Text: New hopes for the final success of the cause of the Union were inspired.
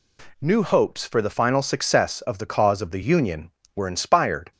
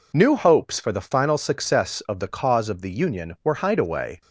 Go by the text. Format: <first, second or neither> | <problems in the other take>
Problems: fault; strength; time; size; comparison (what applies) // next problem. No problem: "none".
first | says "hideaway" for "inspired"; at 3.6 s